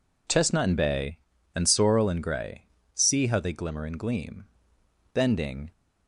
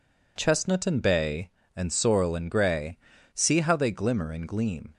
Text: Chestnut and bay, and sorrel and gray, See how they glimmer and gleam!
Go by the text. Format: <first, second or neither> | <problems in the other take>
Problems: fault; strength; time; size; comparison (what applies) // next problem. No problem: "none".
second | goes on to say "Bending"; from 5.1 s on; 0.58 s long